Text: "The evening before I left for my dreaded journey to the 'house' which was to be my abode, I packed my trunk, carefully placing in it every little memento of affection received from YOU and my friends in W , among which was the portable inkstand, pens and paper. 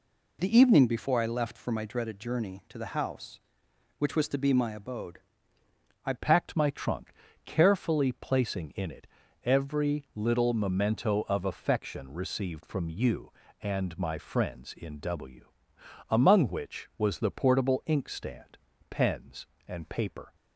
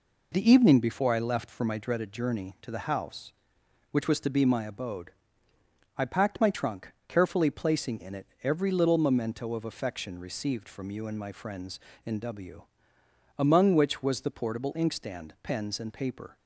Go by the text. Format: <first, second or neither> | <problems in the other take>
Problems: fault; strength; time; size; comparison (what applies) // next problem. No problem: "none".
second | changes voice at "packed"; from 6.1 s on; 14.2 s long // pauses between "it" and "every"; slight; at 9.0 s; 0.36 s long; slight in the second